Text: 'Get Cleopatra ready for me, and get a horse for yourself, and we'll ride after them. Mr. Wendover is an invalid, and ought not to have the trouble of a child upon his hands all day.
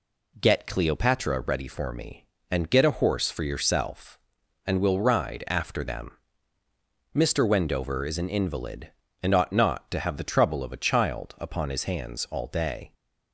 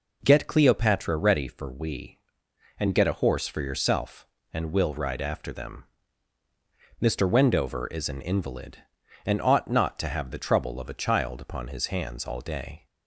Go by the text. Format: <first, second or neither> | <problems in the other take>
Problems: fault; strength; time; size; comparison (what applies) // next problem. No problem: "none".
first | says "we" for "me"; at 1.7 s